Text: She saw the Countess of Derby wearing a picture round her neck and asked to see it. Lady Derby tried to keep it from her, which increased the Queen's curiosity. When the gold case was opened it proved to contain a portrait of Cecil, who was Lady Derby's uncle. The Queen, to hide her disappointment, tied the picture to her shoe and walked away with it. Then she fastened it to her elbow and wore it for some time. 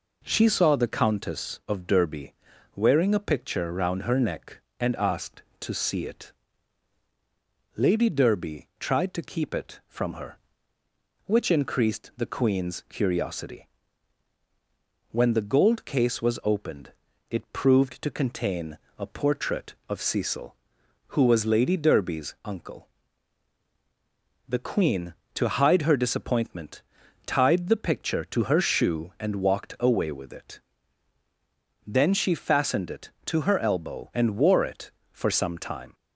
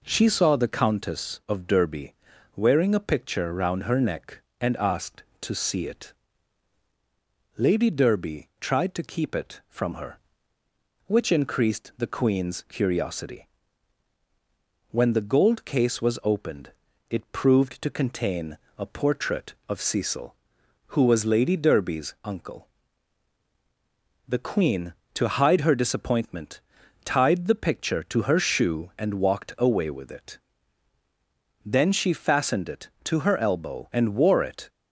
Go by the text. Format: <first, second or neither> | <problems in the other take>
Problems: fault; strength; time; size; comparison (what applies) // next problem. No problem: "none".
first | pauses between "Derby" and "wearing"; at 2.1 s; 0.44 s long; also in the first // pauses between "opened" and "it"; at 16.7 s; 0.38 s long; also in the first // pauses between "contain" and "a"; slight; at 18.5 s; 0.22 s long; slight in the first // stops before "for some time"; at 34.6 s